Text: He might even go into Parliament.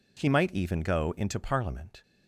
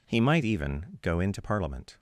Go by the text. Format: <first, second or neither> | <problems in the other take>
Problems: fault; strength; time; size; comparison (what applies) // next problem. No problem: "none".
neither | none